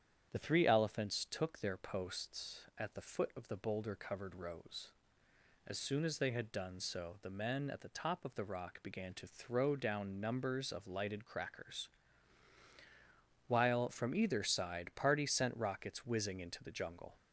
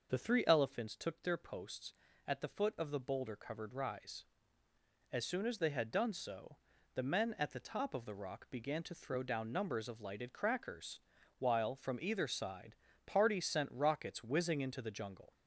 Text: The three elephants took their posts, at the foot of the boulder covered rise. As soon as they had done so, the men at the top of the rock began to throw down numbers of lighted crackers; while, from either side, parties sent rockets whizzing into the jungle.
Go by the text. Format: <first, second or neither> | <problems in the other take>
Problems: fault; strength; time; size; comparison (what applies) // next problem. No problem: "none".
second | starts louder than the rest; strong; until 1.3 s; 9 dB // says "rose" for "rise"; at 4.3 s